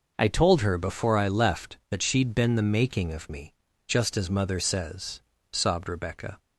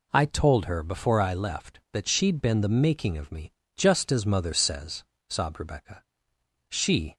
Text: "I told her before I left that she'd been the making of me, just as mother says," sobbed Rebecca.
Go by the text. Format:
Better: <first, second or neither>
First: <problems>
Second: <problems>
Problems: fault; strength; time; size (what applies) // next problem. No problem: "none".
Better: first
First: none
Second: goes on to say "She"; slight; from 6.6 s on; 0.48 s long